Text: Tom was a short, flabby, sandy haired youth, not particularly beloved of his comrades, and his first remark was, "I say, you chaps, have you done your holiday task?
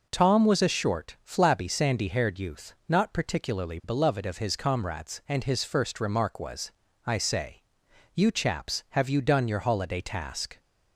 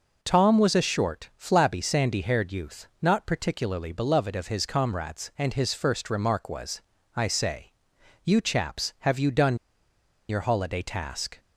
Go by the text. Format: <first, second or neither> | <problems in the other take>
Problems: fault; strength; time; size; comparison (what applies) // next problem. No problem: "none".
first | pauses between "done" and "your"; noticeable; at 9.5 s; 0.71 s long